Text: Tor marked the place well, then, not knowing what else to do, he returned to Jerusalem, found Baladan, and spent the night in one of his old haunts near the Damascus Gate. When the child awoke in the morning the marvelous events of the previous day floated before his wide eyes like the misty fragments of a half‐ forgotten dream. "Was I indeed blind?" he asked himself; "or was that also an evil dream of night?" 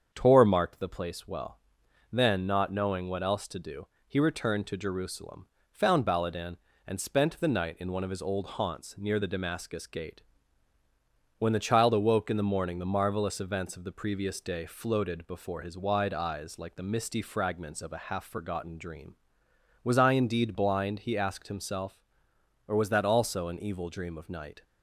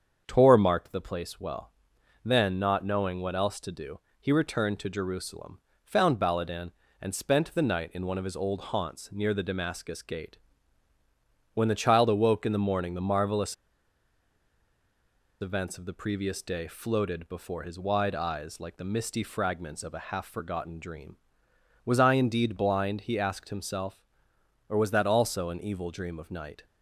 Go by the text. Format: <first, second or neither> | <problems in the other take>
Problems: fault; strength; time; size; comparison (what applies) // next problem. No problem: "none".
first | starts louder than the rest; strong; until 1.2 s; 7.5 dB; strong in the first // pauses between "marvelous" and "events"; strong; at 13.5 s; 1.8 s long